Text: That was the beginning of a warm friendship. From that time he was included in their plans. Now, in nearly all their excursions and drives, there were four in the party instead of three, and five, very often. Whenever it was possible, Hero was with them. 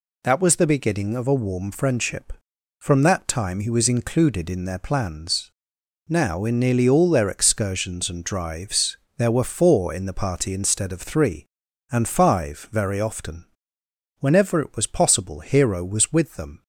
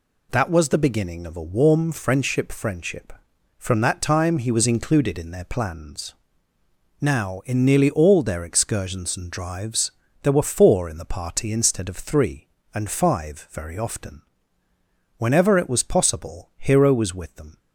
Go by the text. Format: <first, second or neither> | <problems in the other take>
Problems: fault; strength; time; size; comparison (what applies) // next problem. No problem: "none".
first | says "friendship" twice; at 2.5 s